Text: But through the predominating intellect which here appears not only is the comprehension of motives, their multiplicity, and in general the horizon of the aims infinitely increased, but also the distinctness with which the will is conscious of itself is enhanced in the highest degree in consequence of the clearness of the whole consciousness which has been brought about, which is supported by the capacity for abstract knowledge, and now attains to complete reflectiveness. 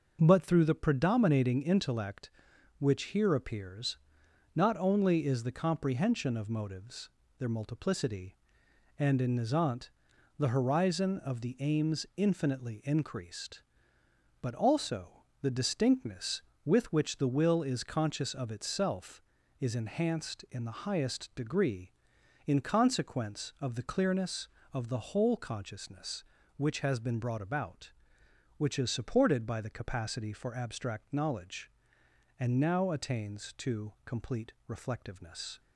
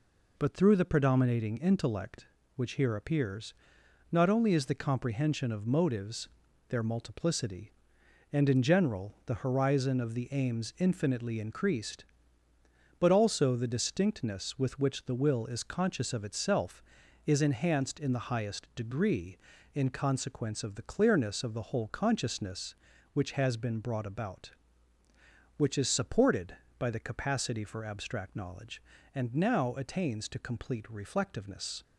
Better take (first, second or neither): second